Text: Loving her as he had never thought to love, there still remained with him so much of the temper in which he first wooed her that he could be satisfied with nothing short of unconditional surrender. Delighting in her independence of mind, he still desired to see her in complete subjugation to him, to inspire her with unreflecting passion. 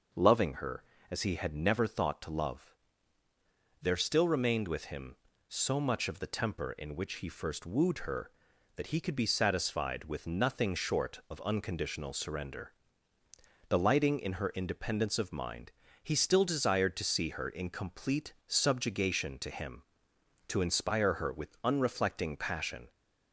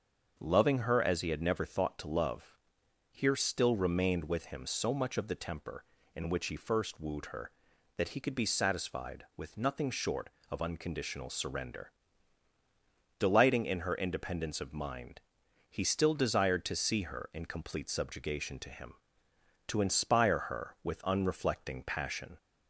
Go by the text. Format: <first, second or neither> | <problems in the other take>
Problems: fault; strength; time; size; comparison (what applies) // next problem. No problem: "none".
first | starts louder than the rest; until 1.3 s; 6.5 dB // says "here" for "there"; at 3.1 s